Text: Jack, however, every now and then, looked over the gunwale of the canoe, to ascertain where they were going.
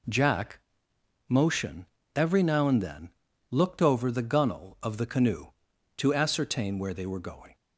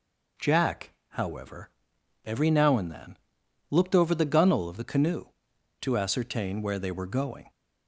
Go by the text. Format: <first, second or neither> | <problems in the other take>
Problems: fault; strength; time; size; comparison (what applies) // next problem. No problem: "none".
second | says "motion" for "however"; at 1.2 s